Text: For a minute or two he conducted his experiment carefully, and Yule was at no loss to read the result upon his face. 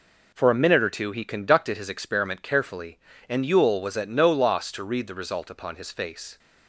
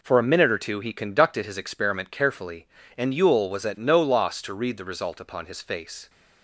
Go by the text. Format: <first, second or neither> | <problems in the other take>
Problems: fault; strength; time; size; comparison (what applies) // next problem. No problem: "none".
neither | none